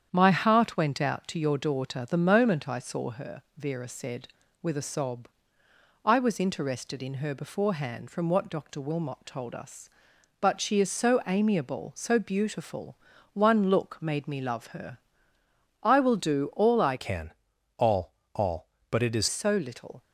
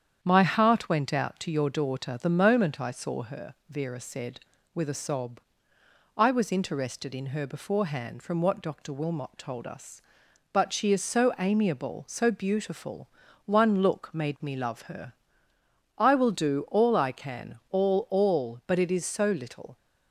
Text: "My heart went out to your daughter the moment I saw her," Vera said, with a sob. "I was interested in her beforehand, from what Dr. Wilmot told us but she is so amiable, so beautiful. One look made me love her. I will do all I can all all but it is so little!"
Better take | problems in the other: second | starts louder than the rest; strong; until 1.1 s; 8.5 dB; strong in the second // changes voice from "can" to "is"; from 16.9 to 19.2 s; 2.3 s long // pauses between "can" and "all"; at 17.3 s; 0.44 s long // pauses between "all" and "all"; slight; at 18.1 s; 0.20 s long

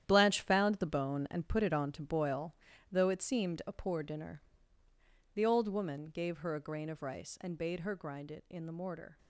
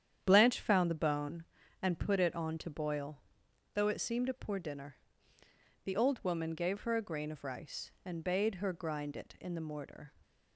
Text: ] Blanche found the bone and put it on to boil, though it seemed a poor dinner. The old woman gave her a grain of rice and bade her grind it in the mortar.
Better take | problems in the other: second | gets quieter; strong; throughout; 10.5 dB // starts louder than the rest; strong; until 1.0 s; 10.5 dB; strong in the second

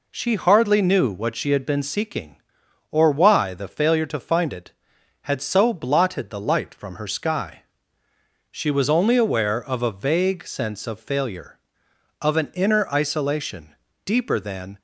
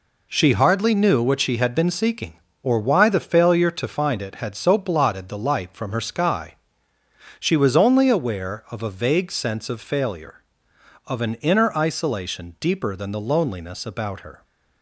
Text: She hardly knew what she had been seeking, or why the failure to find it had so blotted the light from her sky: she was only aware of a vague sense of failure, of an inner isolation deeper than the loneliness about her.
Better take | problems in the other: second | pauses between "isolation" and "deeper"; slight; at 13.7 s; 0.28 s long // stops before "the loneliness about her"; at 14.7 s

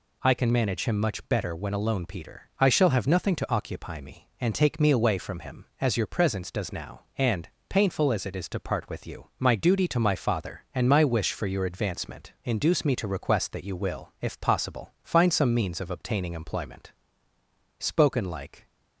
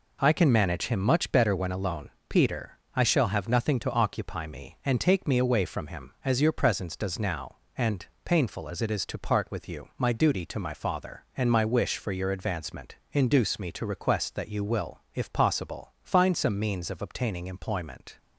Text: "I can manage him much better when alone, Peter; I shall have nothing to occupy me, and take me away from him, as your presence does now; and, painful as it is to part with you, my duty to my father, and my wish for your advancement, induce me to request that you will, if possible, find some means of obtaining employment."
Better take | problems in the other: second | goes on to say "Spoken like"; noticeable; from 17.7 s on; 0.90 s long

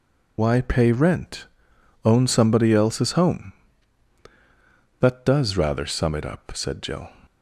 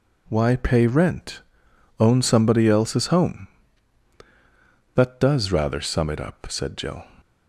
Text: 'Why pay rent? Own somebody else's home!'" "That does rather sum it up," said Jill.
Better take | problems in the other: second | loses the start of "Why"; at 0.3 s; 70 ms

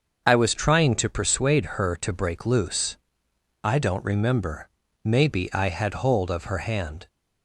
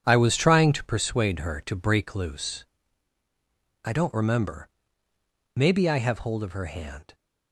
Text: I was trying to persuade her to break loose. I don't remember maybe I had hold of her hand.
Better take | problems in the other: first | starts louder than the rest; strong; until 1.0 s; 8 dB; also in the first // pauses between "remember" and "maybe"; noticeable; at 4.6 s; 0.88 s long; slight in the first // says "have" for "had"; at 5.9 s

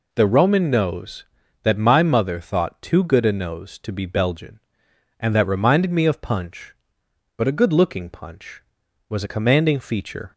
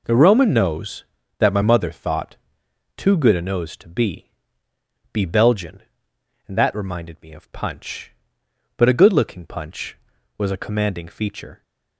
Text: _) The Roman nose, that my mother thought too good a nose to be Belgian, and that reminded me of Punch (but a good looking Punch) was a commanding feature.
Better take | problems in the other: first | pauses between "thought" and "too"; noticeable; at 2.3 s; 0.58 s long // says "be" twice; at 5.1 s

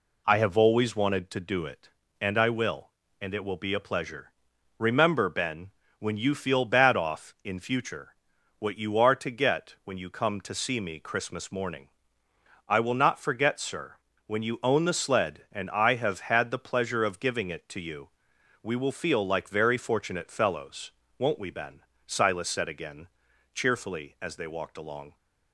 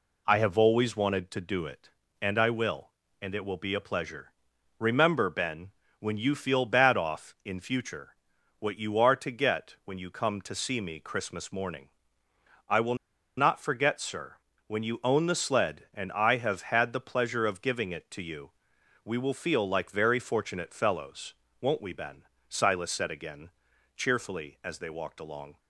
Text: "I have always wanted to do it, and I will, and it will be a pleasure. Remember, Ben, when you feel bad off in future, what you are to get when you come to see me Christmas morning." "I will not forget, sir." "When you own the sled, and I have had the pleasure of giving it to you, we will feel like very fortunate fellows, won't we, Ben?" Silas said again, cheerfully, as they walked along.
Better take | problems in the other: first | pauses between "will" and "not"; at 12.9 s; 0.43 s long

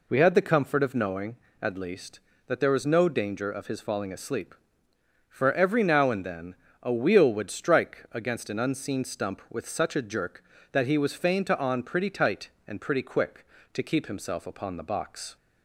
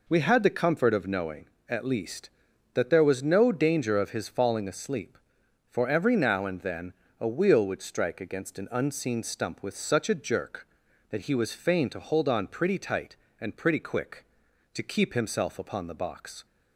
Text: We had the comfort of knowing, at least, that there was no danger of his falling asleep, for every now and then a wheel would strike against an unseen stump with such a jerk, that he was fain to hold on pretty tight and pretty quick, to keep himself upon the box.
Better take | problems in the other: second | pauses between "then" and "a"; slight; at 6.5 s; 0.26 s long; slight in the second // skips "hold"; at 11.5 s

